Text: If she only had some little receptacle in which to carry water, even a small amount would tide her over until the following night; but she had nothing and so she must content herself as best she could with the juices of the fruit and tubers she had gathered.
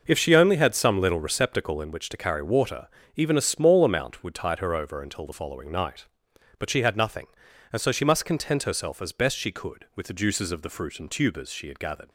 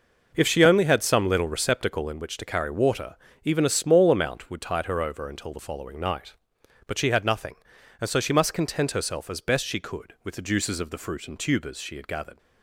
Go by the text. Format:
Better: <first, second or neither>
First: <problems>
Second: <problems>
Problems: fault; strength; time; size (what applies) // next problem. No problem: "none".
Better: neither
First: none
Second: none